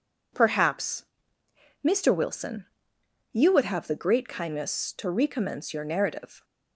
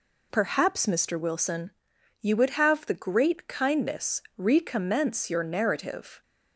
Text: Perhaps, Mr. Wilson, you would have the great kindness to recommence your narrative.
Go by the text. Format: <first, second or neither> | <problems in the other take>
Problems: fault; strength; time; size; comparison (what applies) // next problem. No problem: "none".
first | skips "to"; at 4.2 s